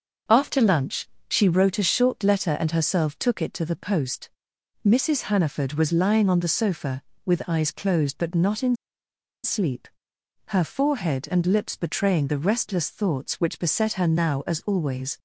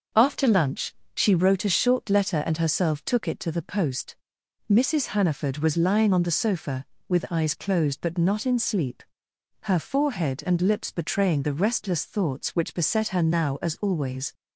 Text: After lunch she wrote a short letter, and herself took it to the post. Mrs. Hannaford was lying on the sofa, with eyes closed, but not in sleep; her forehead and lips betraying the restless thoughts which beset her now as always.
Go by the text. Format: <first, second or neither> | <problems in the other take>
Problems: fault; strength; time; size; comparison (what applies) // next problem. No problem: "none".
second | starts louder than the rest; until 1.5 s; 6.5 dB; also in the second // pauses between "lunch" and "she"; slight; at 1.0 s; 0.22 s long; slight in the second // pauses between "in" and "sleep"; noticeable; at 8.7 s; 0.69 s long